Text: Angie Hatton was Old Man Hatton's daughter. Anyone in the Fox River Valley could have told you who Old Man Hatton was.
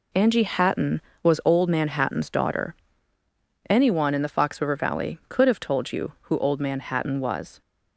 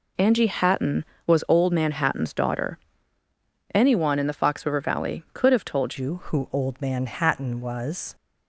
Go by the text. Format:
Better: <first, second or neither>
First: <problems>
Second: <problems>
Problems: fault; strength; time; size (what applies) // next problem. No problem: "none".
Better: first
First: none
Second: changes voice at "you"; from 5.9 s on; 2.2 s long